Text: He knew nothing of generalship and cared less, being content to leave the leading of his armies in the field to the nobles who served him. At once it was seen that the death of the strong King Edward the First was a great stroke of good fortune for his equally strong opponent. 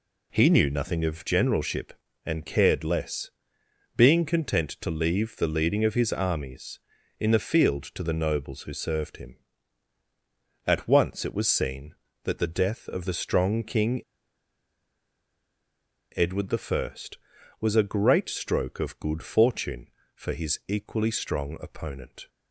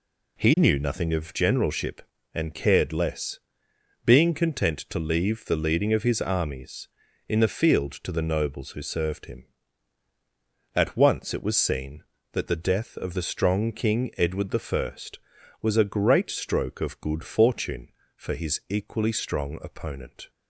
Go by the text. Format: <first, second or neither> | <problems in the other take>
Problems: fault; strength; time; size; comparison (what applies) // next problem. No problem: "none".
second | pauses between "King" and "Edward"; strong; at 14.0 s; 2.1 s long